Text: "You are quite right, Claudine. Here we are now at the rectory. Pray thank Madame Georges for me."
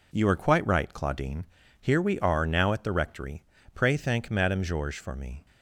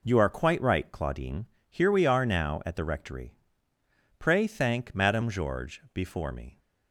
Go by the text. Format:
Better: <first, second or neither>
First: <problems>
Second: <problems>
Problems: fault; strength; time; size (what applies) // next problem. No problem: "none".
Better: first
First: none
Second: says "before" for "for"; at 5.9 s